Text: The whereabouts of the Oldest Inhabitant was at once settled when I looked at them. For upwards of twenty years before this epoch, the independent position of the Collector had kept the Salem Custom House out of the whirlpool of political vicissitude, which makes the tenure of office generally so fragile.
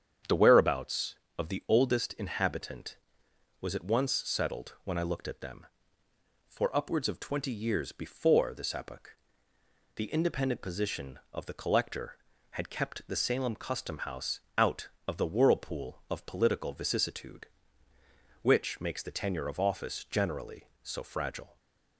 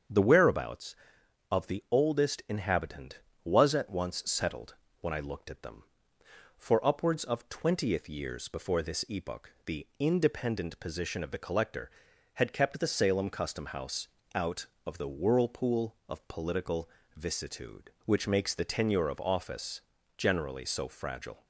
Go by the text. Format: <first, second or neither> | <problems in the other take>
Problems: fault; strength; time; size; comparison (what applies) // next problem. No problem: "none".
first | starts louder than the rest; strong; until 1.6 s; 7.5 dB; strong in the first // pauses between "settled" and "when"; slight; at 4.7 s; 0.26 s long // says "twentieth" for "twenty"; at 7.4 s // pauses between "House" and "out"; slight; at 14.0 s; 0.26 s long; slight in the first // pauses between "political" and "vicissitude"; slight; at 16.8 s; 0.28 s long // pauses between "office" and "generally"; at 19.8 s; 0.38 s long